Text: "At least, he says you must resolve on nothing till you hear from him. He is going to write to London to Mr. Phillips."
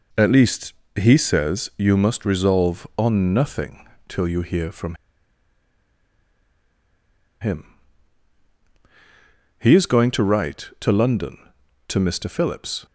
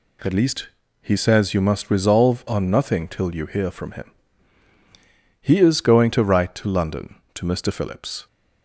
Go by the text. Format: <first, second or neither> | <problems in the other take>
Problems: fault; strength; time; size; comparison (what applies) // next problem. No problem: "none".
second | pauses between "nothing" and "till"; slight; at 3.8 s; 0.22 s long // pauses between "from" and "him"; strong; at 4.9 s; 2.4 s long